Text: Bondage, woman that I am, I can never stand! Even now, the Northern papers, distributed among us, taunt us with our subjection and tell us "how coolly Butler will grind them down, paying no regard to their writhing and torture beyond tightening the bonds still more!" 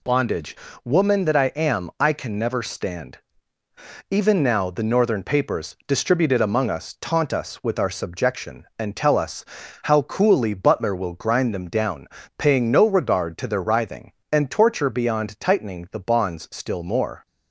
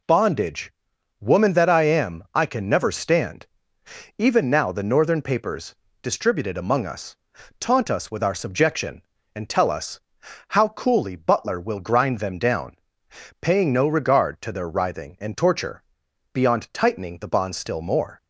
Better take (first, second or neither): first